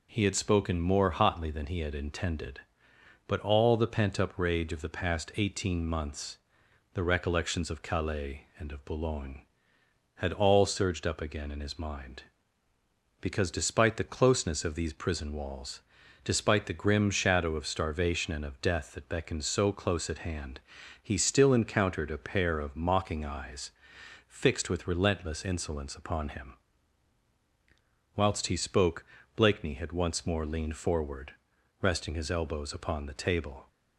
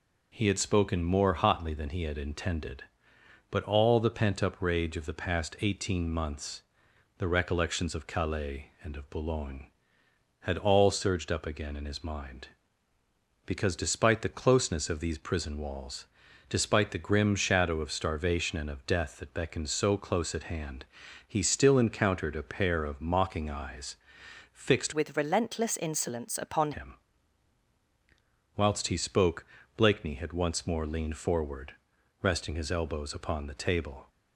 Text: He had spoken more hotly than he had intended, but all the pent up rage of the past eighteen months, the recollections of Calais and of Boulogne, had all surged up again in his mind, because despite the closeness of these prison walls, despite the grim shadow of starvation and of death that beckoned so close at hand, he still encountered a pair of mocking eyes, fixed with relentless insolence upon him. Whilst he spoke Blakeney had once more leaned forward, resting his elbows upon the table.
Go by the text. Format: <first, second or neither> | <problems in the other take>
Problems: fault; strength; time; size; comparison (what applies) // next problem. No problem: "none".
first | changes voice from "with" to "upon"; from 24.9 to 26.7 s; 1.8 s long // pauses between "spoke" and "Blakeney"; slight; at 29.4 s; 0.32 s long; slight in the first